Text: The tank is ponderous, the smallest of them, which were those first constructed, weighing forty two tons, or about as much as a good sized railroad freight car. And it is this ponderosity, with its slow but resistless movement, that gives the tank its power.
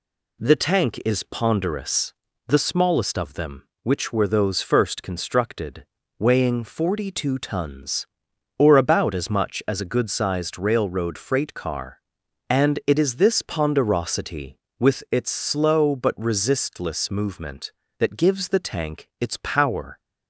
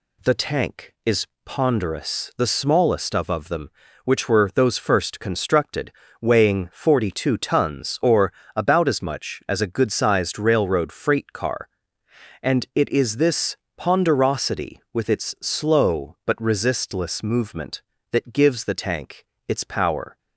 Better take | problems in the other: first | pauses between "is" and "ponderous"; slight; at 1.2 s; 0.18 s long // says "of" twice; at 3.2 s // pauses between "or" and "about"; slight; at 8.3 s; 0.20 s long // pauses between "this" and "ponderosity"; slight; at 13.5 s; 0.22 s long // pauses between "tank" and "its"; slight; at 19.2 s; 0.24 s long

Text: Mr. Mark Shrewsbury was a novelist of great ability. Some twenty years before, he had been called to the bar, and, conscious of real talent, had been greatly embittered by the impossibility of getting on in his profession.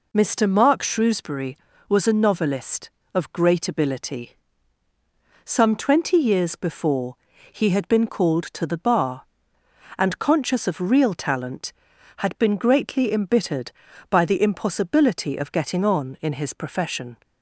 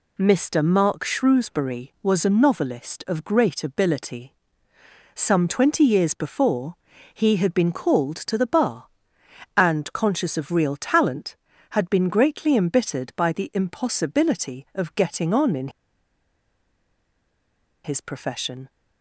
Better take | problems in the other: first | pauses between "in" and "his"; strong; at 15.6 s; 2.1 s long

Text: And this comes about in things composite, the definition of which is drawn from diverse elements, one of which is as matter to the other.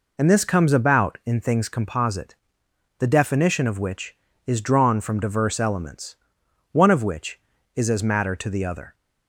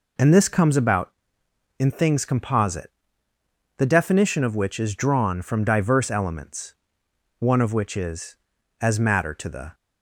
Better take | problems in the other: first | stops before "other"; at 9.7 s

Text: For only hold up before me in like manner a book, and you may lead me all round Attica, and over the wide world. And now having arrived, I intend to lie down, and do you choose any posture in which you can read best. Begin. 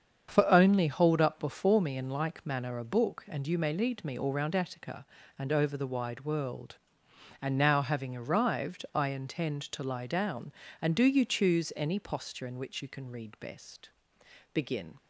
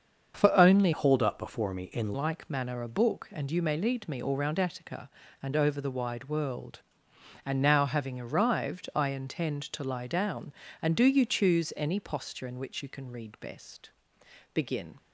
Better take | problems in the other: first | starts louder than the rest; until 1.3 s; 7 dB; strong in the first // changes voice from "hold" to "in"; from 0.9 to 2.1 s; 1.2 s long

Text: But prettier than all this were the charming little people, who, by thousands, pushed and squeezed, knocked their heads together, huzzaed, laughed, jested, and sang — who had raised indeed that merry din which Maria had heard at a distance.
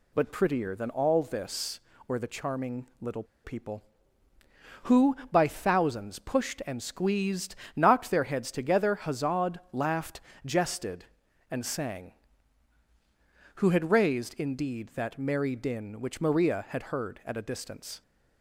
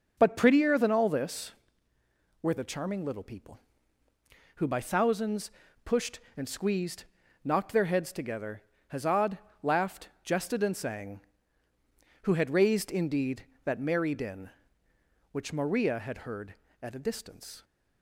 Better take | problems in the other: second | pauses between "little" and "people"; slight; at 3.2 s; 0.20 s long

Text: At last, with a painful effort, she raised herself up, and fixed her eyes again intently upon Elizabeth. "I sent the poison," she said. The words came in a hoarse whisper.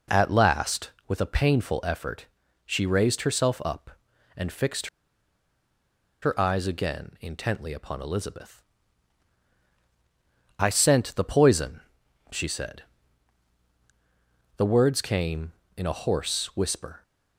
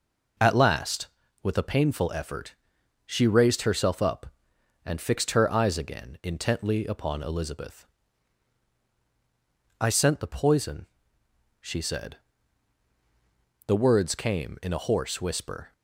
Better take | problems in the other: second | pauses between "fixed" and "her"; strong; at 4.8 s; 1.3 s long

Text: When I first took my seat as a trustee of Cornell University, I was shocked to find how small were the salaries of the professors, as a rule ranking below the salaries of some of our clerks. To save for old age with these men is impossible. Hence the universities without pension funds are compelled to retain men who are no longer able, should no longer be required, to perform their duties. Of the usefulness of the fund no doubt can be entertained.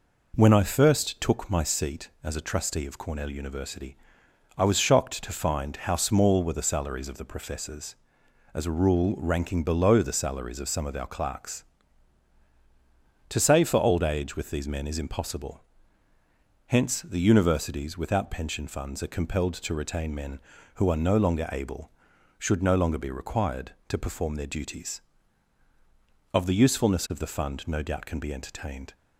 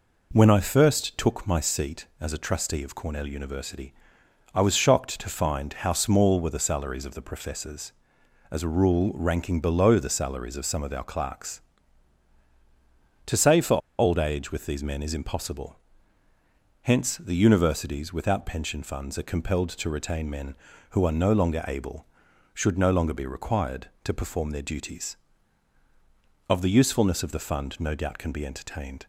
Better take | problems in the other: first | pauses between "for" and "old"; slight; at 13.7 s; 0.20 s long

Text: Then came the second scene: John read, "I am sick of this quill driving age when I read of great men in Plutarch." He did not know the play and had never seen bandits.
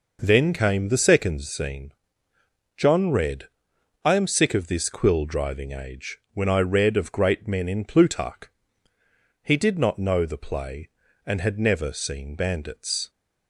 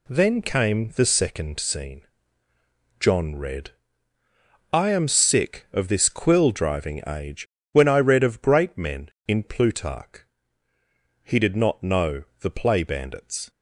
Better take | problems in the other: first | pauses between "age" and "when"; slight; at 7.4 s; 0.24 s long; slight in the first // pauses between "know" and "the"; slight; at 12.2 s; 0.18 s long // skips "and had never seen"; at 12.8 s

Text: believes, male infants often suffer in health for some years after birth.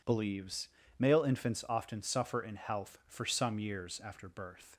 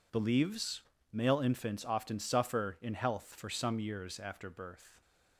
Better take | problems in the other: neither | none

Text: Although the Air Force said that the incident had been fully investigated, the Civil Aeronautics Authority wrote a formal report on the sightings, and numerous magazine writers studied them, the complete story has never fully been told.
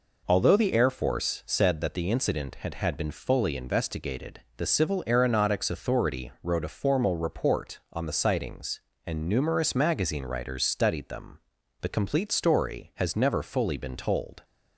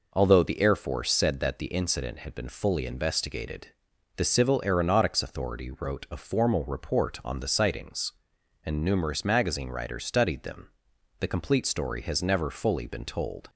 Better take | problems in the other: second | says "had" twice; at 2.7 s

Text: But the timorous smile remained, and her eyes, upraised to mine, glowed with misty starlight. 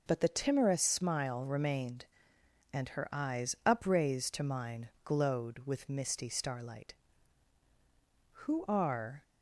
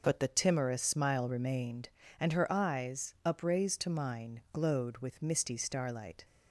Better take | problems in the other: second | goes on to say "Who are"; noticeable; from 8.3 s on; 0.92 s long

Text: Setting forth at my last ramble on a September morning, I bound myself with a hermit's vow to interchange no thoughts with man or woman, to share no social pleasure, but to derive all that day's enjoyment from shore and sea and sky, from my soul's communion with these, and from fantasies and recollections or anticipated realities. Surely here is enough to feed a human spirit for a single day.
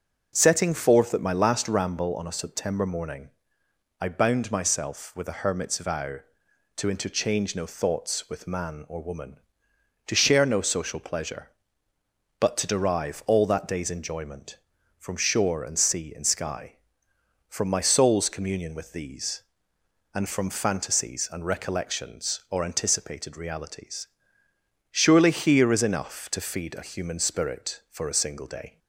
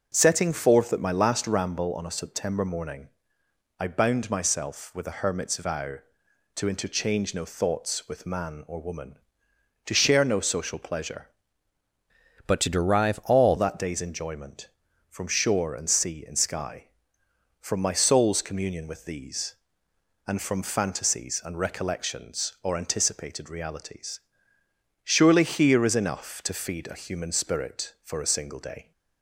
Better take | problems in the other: first | changes voice from "but" to "all"; from 12.4 to 13.5 s; 1.1 s long

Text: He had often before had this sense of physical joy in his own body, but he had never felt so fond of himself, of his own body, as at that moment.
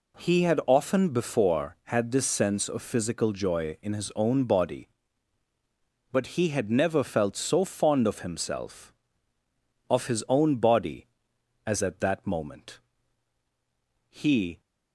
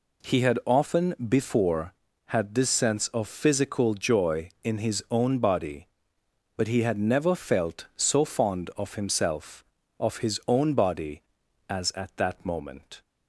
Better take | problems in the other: second | goes on to say "He"; from 14.0 s on; 0.52 s long

